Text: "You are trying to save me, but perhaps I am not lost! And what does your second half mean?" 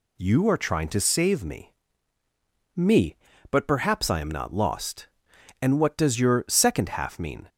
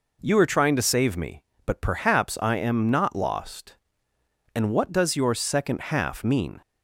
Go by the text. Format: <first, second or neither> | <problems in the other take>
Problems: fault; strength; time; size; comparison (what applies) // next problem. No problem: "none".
second | says "me" twice; at 2.7 s